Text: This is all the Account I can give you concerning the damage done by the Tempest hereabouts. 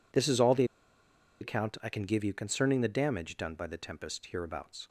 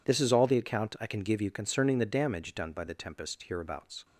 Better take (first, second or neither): second